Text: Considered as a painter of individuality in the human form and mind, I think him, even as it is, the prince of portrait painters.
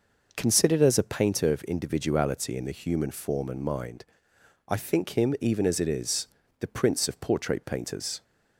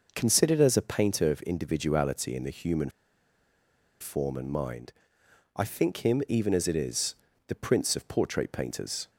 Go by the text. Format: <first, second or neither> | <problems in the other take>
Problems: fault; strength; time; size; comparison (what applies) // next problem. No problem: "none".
first | pauses between "human" and "form"; at 2.8 s; 1.1 s long